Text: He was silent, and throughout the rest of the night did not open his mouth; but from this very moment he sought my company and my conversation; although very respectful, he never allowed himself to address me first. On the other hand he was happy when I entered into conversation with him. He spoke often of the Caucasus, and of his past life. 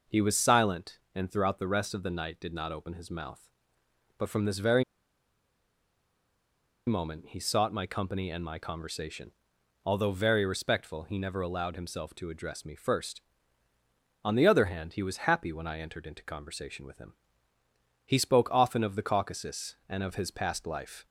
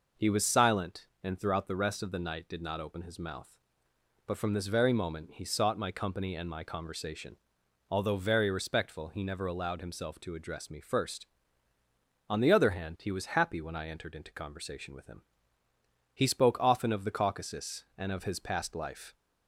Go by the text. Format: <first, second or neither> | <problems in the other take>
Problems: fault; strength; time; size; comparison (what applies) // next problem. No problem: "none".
second | pauses between "very" and "moment"; strong; at 4.8 s; 2.0 s long